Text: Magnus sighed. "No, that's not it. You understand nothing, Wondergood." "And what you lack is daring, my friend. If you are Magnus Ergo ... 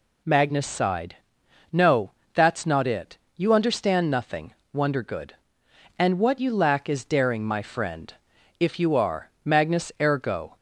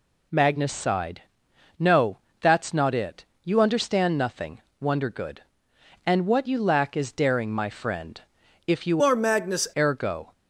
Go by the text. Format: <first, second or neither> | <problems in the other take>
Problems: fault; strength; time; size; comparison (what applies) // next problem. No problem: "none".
first | changes voice from "are" to "Magnus"; from 9.0 to 9.6 s; 0.6 s long